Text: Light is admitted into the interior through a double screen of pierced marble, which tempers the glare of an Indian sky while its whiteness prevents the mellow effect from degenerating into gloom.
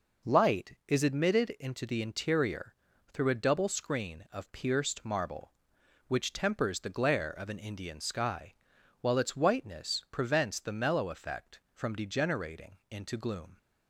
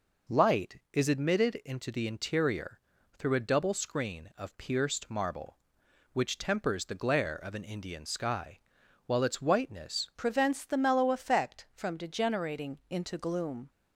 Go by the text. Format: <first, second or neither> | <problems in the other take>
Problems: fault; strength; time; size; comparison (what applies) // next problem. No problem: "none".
first | pauses between "interior" and "through"; slight; at 2.8 s; 0.36 s long; slight in the first // pauses between "sky" and "while"; noticeable; at 8.5 s; 0.48 s long; noticeable in the first // changes voice at "prevents"; from 10.1 s on; 3.6 s long